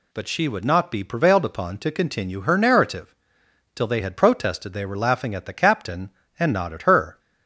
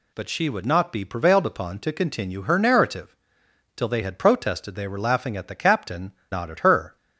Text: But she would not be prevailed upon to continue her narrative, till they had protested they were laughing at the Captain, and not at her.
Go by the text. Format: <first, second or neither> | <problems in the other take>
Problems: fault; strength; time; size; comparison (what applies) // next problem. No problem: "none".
first | skips "and"; at 6.2 s